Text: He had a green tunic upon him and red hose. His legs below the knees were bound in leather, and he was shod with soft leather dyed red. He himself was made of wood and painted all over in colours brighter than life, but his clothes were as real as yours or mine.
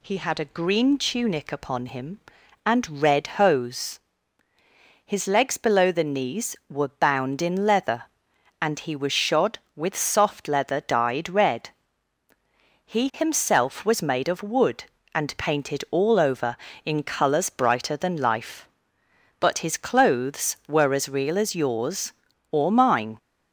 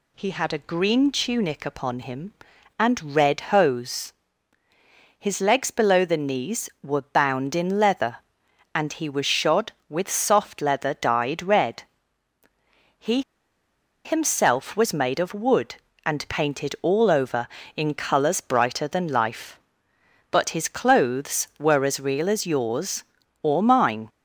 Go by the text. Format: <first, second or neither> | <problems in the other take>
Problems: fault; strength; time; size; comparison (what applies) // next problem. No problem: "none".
first | pauses between "He" and "himself"; noticeable; at 13.2 s; 0.83 s long